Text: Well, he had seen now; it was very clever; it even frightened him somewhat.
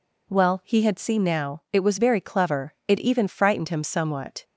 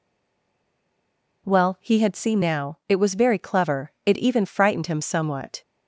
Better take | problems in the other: first | stays silent before the first word; noticeable; until 1.4 s; 1.4 s long

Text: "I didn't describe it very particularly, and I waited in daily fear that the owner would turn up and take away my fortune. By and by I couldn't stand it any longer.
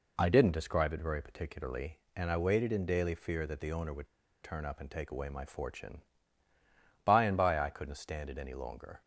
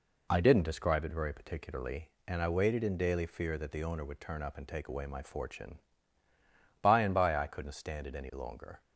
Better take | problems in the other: second | pauses between "would" and "turn"; slight; at 4.0 s; 0.35 s long

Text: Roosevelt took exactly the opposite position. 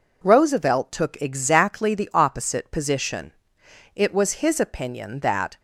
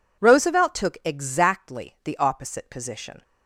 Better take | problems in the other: second | goes on to say "It was his opinion that"; from 3.9 s on; 1.6 s long

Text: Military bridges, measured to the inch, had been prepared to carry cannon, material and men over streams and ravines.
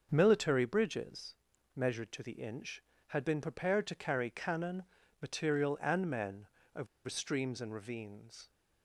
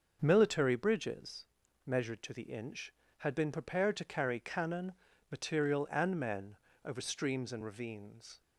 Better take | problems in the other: second | starts louder than the rest; until 1.1 s; 6.5 dB; also in the second // pauses between "men" and "over"; slight; at 6.4 s; 0.26 s long; slight in the second // pauses between "over" and "streams"; slight; at 6.8 s; 0.20 s long

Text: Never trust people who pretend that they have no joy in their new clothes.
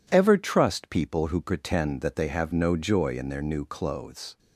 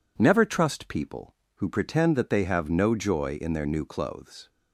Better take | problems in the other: second | says "Ever" for "Never"; at 0.1 s

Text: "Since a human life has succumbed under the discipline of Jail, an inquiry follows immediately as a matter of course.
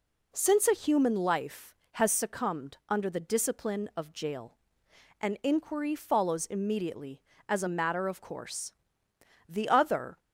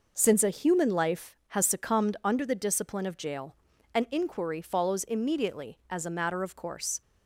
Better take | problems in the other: second | goes on to say "The other"; noticeable; from 9.4 s on; 0.70 s long

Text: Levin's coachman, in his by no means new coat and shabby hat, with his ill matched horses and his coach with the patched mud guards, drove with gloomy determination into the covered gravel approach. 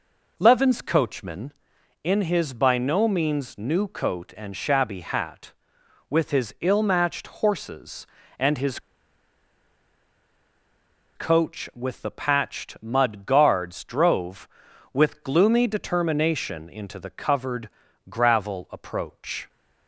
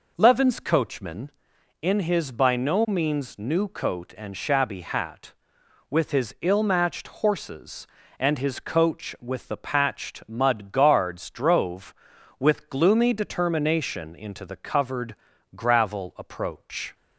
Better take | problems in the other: second | pauses between "his" and "coach"; strong; at 8.7 s; 2.3 s long // pauses between "covered" and "gravel"; at 17.6 s; 0.40 s long; also in the second

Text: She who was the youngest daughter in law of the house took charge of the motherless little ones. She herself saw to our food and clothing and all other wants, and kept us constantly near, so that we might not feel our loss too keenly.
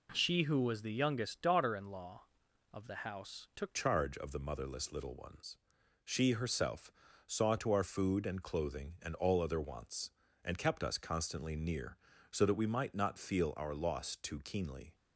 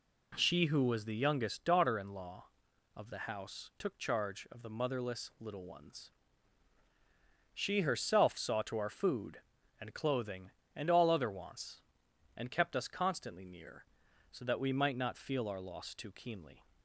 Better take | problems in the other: second | changes voice at "charge"; from 3.7 s on; 11.2 s long // pauses between "herself" and "saw"; slight; at 6.9 s; 0.36 s long

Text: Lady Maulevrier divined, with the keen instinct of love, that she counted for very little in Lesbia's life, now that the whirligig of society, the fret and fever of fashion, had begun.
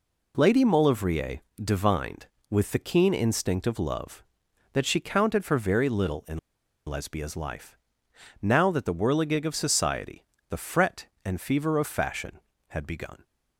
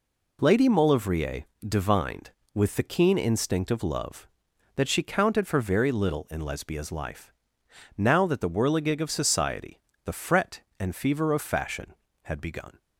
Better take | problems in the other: second | pauses between "Maulevrier" and "divined"; slight; at 1.3 s; 0.24 s long; slight in the second // pauses between "in" and "Lesbia's"; noticeable; at 6.3 s; 0.48 s long

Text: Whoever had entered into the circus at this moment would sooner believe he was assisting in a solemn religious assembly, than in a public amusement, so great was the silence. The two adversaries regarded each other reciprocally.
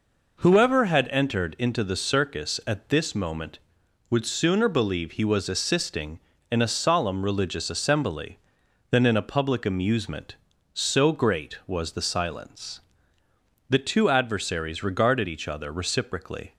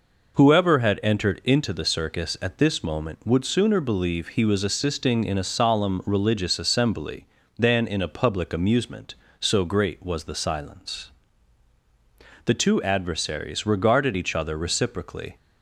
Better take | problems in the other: neither | none

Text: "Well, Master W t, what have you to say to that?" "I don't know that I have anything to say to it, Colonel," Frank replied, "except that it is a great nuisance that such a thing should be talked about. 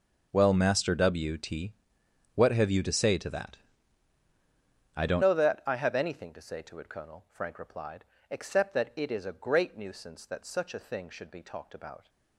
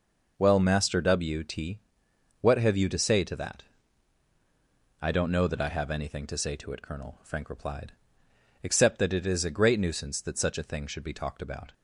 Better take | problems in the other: second | changes voice at "know"; from 5.2 s on; 6.8 s long

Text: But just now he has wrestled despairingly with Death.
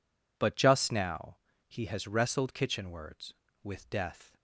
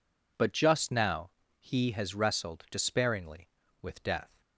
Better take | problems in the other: second | pauses between "now" and "he"; slight; at 1.3 s; 0.30 s long; slight in the second // says "kitchenwards" for "despairingly"; at 2.5 s

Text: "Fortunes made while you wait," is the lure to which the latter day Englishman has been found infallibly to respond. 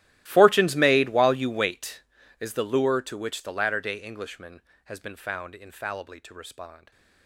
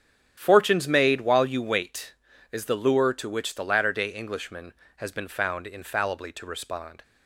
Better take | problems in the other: second | gets quieter; strong; throughout; 22.5 dB // starts louder than the rest; strong; until 1.2 s; 15.5 dB; strong in the second

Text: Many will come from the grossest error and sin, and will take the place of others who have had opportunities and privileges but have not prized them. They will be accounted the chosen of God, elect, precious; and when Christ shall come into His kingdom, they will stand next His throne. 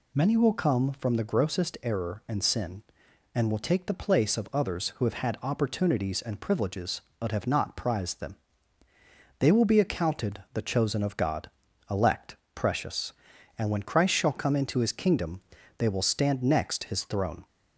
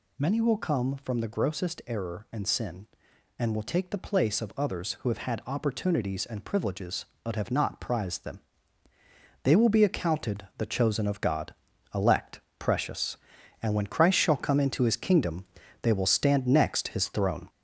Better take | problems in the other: first | gets louder; throughout; 4 dB

